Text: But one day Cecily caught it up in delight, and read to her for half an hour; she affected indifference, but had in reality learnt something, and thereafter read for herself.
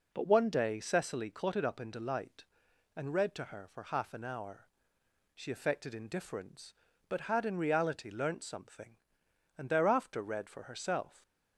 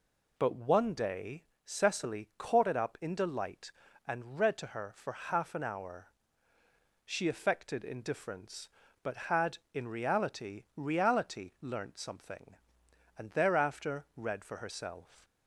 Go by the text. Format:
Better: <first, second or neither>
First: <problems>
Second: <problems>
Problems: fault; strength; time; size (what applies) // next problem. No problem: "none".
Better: first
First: none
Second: pauses between "day" and "Cecily"; slight; at 1.4 s; 0.20 s long // says "reality" twice; at 10.7 s